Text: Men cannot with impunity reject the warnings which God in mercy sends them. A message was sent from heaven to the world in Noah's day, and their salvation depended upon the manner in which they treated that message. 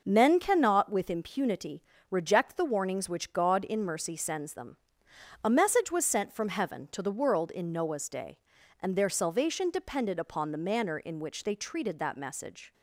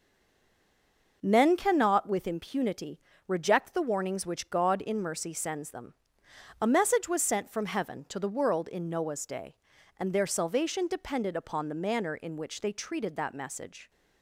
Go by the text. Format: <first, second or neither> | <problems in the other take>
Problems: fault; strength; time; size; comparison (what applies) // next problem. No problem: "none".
first | stays silent before the first word; noticeable; until 1.2 s; 1.2 s long // pauses between "impunity" and "reject"; slight; at 2.9 s; 0.26 s long; slight in the first